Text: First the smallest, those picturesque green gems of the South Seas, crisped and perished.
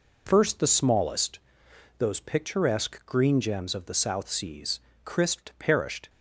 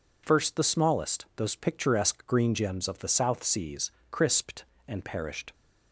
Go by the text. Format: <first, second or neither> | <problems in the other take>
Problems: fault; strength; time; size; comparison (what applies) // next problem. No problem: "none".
second | skips "and"; at 5.5 s